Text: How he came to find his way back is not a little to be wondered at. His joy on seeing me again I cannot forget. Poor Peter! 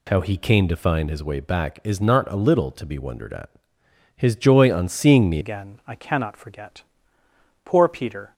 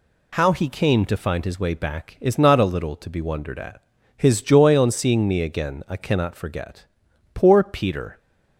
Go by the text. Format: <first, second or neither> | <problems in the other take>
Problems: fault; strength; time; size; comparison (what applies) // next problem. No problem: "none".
second | changes voice at "again"; from 5.4 s on; 2.9 s long